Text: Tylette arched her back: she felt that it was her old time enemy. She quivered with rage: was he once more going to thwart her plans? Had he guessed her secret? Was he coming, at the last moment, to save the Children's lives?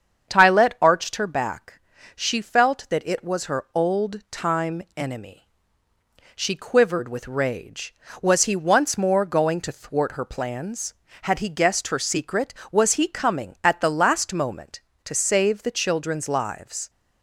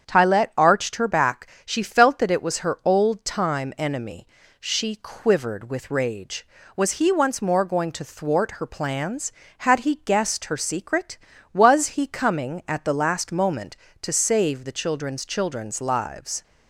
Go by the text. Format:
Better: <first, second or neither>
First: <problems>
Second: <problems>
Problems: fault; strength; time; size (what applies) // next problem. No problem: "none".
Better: first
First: starts louder than the rest; strong; until 1.3 s; 7.5 dB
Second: starts louder than the rest; strong; until 1.0 s; 7.5 dB // says "Children's" twice; at 15.2 s